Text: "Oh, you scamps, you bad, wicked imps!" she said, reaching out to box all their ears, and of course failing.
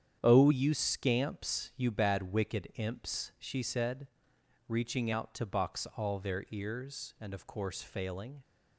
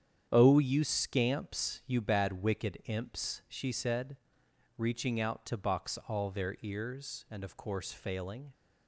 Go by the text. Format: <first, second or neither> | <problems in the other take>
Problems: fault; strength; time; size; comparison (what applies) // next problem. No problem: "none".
neither | starts louder than the rest; strong; the same in both